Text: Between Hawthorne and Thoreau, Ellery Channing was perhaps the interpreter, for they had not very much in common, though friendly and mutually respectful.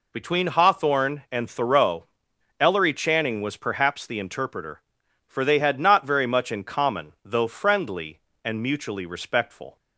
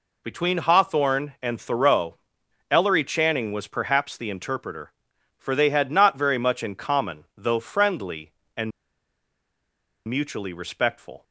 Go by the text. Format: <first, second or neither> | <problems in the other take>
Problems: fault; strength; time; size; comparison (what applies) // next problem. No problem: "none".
first | pauses between "and" and "mutually"; strong; at 8.7 s; 1.3 s long